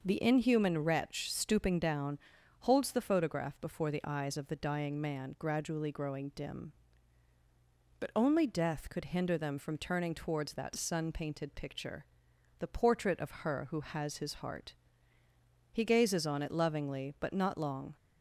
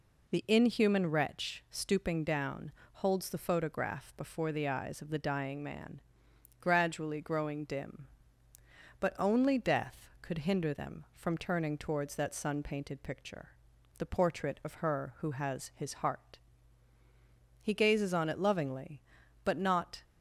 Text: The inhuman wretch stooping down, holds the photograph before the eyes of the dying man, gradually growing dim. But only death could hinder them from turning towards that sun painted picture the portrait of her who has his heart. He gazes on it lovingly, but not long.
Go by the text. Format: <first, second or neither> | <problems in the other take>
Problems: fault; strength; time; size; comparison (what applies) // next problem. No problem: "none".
first | pauses between "picture" and "the"; noticeable; at 13.4 s; 0.50 s long; noticeable in the first // stops before "long"; at 20.0 s